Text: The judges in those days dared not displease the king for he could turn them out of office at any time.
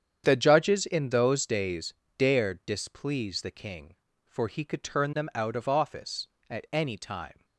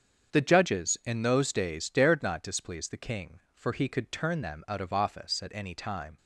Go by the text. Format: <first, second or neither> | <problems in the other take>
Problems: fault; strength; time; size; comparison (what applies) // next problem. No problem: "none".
second | starts louder than the rest; strong; until 1.2 s; 8.5 dB; strong in the second // pauses between "days" and "dared"; slight; at 1.9 s; 0.24 s long // skips "not"; at 2.6 s